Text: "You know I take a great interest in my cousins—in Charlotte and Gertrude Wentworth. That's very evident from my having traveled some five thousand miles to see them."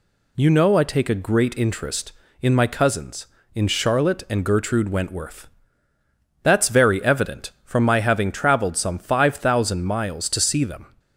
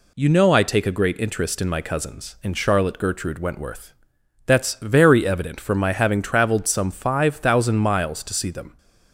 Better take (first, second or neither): first